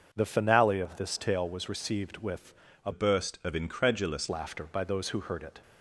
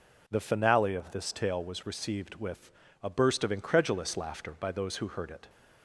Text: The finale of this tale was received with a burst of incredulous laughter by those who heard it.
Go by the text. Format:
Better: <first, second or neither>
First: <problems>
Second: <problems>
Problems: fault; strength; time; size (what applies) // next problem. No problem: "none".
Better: second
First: starts louder than the rest; until 1.1 s; 6.5 dB // pauses between "with" and "a"; slight; at 2.5 s; 0.30 s long // changes voice from "burst" to "incredulous"; from 2.9 to 4.2 s; 1.3 s long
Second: pauses between "with" and "a"; slight; at 2.7 s; 0.30 s long